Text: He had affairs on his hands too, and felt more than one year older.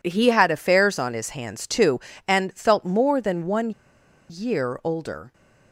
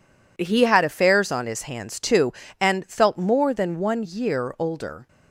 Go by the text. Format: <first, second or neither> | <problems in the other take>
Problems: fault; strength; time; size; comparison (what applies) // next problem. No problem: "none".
second | pauses between "one" and "year"; noticeable; at 3.7 s; 0.59 s long